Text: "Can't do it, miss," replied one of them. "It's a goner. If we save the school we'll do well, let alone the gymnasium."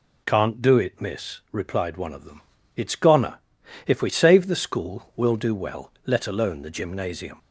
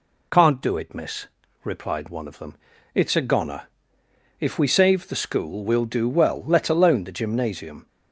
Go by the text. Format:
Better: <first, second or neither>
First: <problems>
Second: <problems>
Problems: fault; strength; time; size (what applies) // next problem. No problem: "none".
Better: second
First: skips "a"; at 2.9 s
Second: none